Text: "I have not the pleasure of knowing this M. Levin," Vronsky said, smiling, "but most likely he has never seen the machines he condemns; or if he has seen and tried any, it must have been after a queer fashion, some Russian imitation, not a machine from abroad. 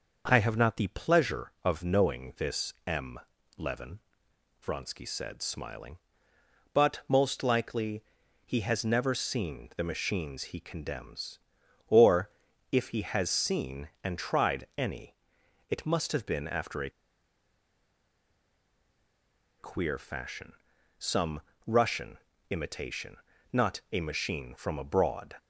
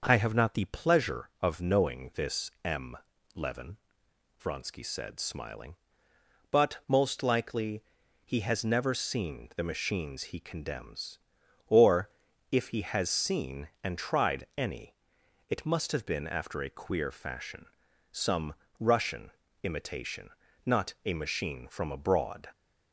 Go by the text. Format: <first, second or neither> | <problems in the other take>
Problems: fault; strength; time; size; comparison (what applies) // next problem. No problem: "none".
second | pauses between "likely" and "he"; at 8.0 s; 0.42 s long; also in the second // pauses between "or" and "if"; at 12.2 s; 0.44 s long; also in the second // pauses between "a" and "queer"; strong; at 16.9 s; 2.6 s long // pauses between "some" and "Russian"; slight; at 21.4 s; 0.24 s long; slight in the second // pauses between "Russian" and "imitation"; slight; at 22.1 s; 0.32 s long; slight in the second